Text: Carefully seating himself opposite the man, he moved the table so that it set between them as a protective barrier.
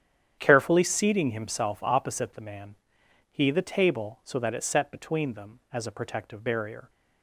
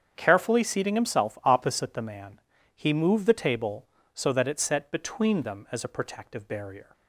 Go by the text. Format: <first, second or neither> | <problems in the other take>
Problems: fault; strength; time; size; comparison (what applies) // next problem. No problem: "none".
second | starts louder than the rest; strong; until 1.4 s; 9.5 dB; strong in the second // skips "moved"; at 3.4 s